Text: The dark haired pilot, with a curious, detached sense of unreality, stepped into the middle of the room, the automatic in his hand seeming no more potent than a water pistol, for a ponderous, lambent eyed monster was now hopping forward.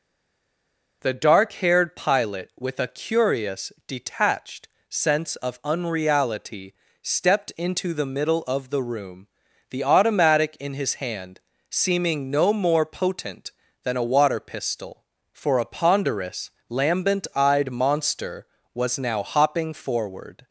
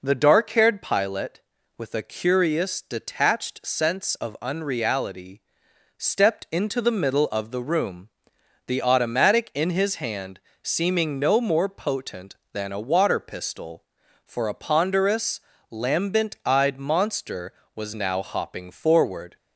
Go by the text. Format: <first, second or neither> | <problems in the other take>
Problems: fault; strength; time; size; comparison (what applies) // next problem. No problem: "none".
second | stays silent before the first word; until 1.0 s; 1.0 s long // pauses between "detached" and "sense"; slight; at 4.6 s; 0.22 s long // pauses between "hand" and "seeming"; slight; at 11.3 s; 0.30 s long; slight in the second